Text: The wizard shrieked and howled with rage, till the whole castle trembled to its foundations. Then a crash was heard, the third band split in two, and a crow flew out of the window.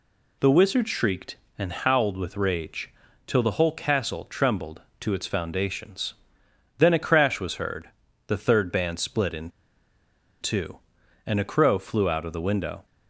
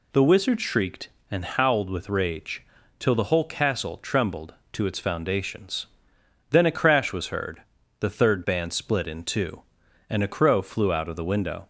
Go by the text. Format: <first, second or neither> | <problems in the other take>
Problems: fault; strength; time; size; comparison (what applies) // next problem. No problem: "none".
second | pauses between "in" and "two"; noticeable; at 9.4 s; 0.92 s long